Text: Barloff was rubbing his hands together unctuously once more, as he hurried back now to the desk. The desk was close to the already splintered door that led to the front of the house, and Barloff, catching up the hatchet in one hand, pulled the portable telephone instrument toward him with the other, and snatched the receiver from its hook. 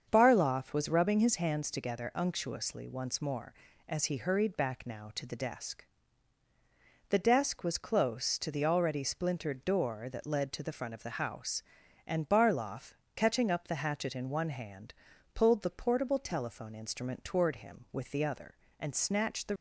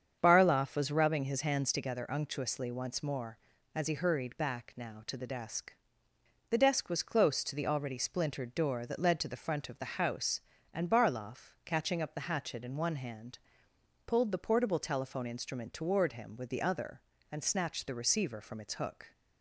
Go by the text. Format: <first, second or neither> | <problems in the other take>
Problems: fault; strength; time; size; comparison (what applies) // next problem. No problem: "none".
second | starts louder than the rest; until 1.1 s; 7 dB; strong in the second // stops before "receiver from its hook"; at 19.5 s